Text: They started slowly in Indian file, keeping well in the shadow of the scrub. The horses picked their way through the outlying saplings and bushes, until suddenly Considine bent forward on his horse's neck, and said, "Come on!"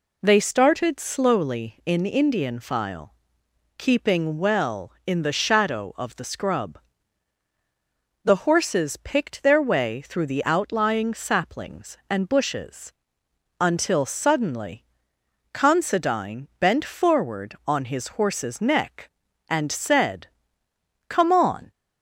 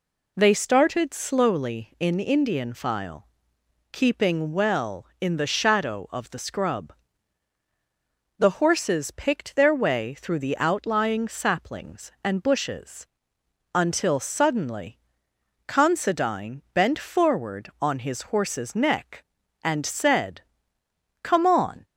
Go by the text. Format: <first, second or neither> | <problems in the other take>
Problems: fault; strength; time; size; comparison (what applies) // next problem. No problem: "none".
neither | pauses between "suddenly" and "Considine"; noticeable; the same in both